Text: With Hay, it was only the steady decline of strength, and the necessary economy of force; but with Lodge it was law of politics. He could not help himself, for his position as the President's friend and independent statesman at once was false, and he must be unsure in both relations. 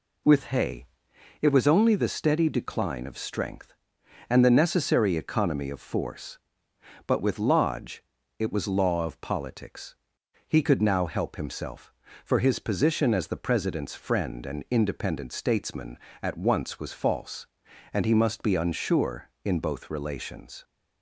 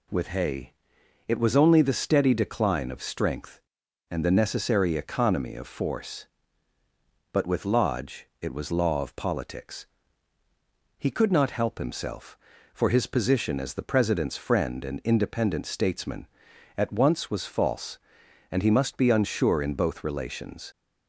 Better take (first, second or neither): second